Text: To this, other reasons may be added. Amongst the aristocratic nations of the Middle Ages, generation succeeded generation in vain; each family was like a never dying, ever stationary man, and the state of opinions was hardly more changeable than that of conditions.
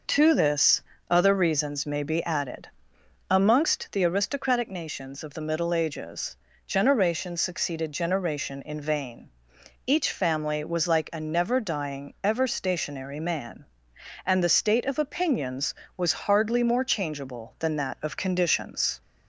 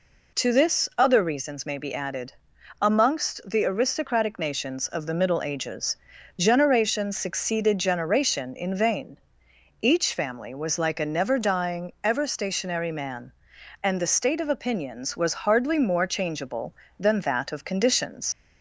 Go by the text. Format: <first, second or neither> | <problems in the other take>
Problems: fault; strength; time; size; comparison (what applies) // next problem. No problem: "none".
first | leaves "conditions" unfinished; at 18.3 s; 65 ms